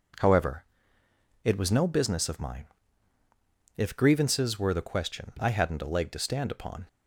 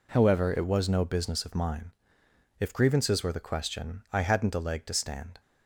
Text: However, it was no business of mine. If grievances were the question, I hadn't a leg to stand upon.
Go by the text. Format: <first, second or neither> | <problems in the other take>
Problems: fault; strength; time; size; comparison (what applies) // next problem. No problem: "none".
first | stops before "upon"; at 5.3 s